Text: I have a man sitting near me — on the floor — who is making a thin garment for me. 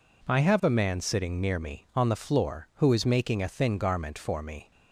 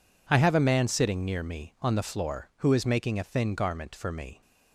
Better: neither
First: none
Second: none

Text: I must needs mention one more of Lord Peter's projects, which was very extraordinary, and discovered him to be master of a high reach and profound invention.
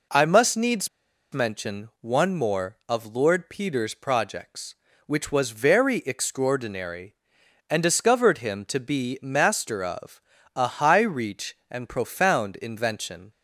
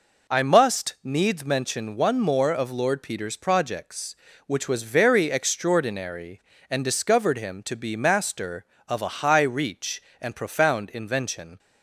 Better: second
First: pauses between "needs" and "mention"; at 0.8 s; 0.43 s long // pauses between "of" and "a"; slight; at 10.2 s; 0.36 s long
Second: none

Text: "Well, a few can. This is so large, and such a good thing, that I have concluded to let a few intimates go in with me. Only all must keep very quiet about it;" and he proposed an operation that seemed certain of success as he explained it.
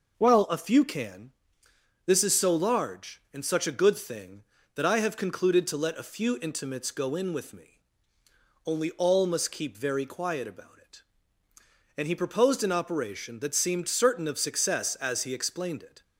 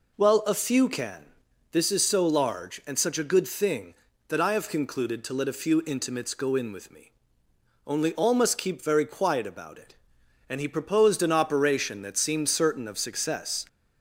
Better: first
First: none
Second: stops before "as he explained it"; at 13.6 s

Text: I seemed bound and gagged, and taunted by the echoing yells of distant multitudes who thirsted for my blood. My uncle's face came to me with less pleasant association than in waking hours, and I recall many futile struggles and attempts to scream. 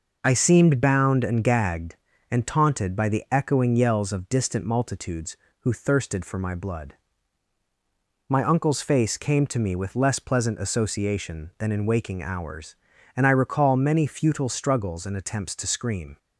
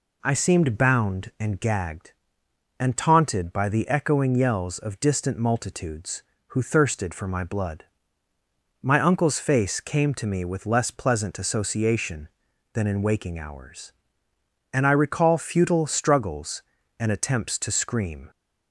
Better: first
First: none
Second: skips "many"; at 15.3 s

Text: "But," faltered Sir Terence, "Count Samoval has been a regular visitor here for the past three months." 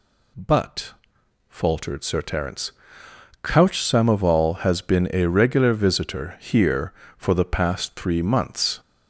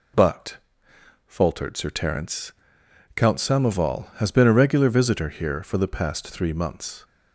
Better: second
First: says "Couch" for "Count"; at 3.4 s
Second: none

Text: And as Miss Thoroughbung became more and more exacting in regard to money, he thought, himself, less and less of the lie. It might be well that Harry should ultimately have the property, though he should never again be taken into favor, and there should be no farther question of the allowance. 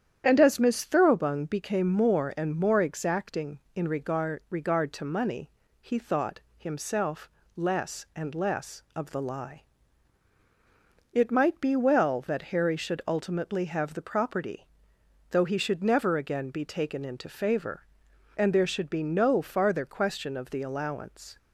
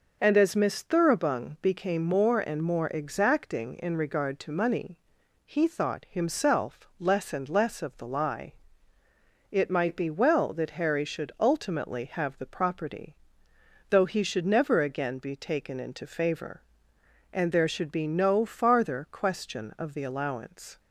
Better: second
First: starts louder than the rest; strong; until 1.2 s; 9.5 dB // says "regard" twice; at 4.4 s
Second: none

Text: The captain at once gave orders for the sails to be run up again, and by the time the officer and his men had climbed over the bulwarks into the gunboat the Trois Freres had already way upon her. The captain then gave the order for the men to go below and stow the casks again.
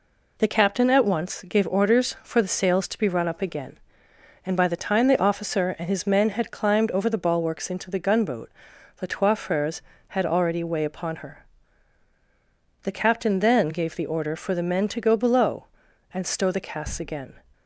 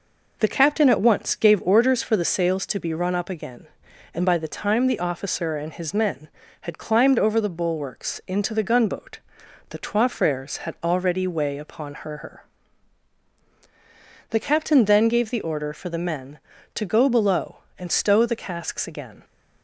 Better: first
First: pauses between "gunboat" and "the"; noticeable; at 8.5 s; 0.46 s long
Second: pauses between "gunboat" and "the"; noticeable; at 9.1 s; 0.50 s long // says "her" twice; at 12.1 s

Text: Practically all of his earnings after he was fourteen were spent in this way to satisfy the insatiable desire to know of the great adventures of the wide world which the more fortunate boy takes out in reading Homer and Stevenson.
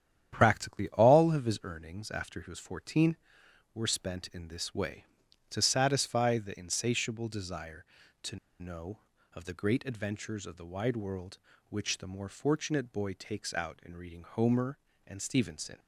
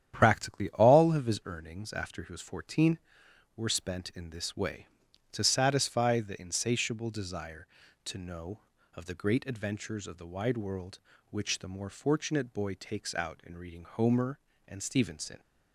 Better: second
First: starts louder than the rest; strong; until 1.3 s; 10 dB // pauses between "to" and "know"; slight; at 8.3 s; 0.24 s long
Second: starts louder than the rest; strong; until 1.1 s; 10 dB

